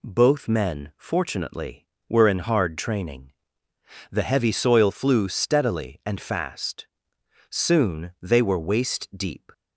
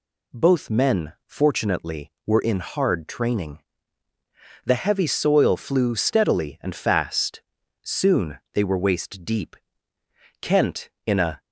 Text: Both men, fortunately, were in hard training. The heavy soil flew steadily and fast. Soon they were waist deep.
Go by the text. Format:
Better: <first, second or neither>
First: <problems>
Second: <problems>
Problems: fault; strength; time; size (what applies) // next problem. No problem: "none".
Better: first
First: none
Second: pauses between "Soon" and "they"; slight; at 8.3 s; 0.16 s long // goes on to say "Kent in a"; noticeable; from 10.3 s on; 1.0 s long